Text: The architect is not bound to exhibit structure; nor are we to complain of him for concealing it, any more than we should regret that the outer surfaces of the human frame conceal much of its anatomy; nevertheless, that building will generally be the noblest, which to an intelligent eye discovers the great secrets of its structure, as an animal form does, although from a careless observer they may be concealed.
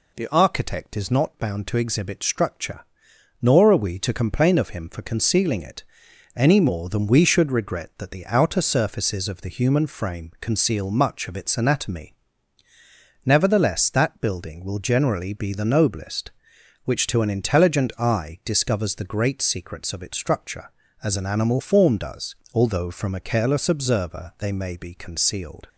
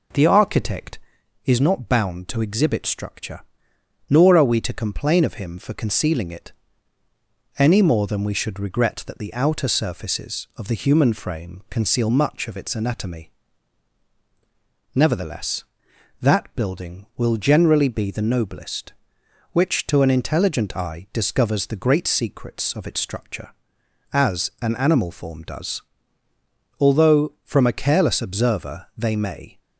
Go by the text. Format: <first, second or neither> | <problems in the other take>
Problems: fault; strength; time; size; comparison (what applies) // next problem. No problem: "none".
first | stops before "be concealed"; at 29.5 s